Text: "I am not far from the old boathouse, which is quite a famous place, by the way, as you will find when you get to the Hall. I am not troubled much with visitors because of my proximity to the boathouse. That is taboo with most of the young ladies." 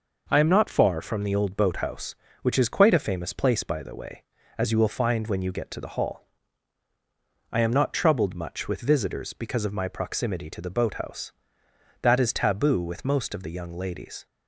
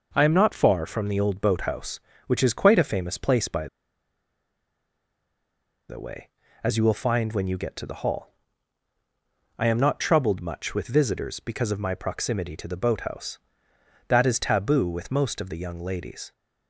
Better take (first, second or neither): first